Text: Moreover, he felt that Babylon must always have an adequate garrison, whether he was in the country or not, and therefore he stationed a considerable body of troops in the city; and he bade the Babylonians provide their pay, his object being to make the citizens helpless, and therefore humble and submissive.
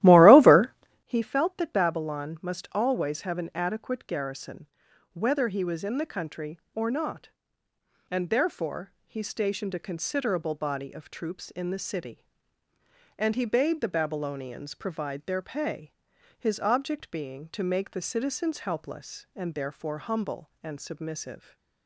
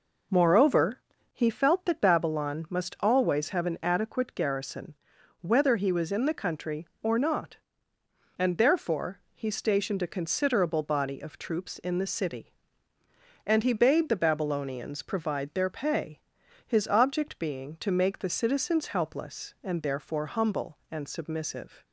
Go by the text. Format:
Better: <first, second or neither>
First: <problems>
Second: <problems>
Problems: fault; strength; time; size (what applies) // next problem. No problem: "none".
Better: second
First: starts louder than the rest; strong; until 1.1 s; 15 dB // pauses between "therefore" and "he"; slight; at 8.9 s; 0.16 s long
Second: pauses between "therefore" and "he"; slight; at 9.1 s; 0.16 s long